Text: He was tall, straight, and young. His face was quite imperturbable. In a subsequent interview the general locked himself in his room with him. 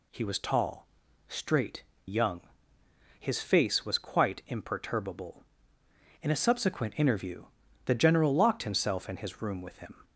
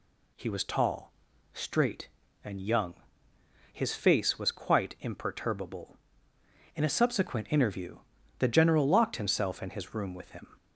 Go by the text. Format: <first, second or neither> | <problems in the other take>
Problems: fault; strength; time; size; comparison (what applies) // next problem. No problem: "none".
second | skips "and"; at 1.9 s // pauses between "interview" and "the"; at 7.4 s; 0.40 s long; also in the second